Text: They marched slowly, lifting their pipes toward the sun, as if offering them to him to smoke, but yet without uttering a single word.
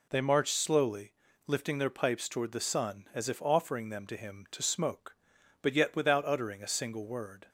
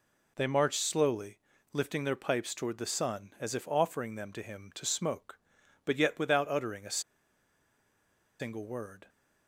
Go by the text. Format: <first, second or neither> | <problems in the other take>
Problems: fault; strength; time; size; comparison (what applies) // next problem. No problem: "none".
first | pauses between "a" and "single"; strong; at 6.9 s; 1.3 s long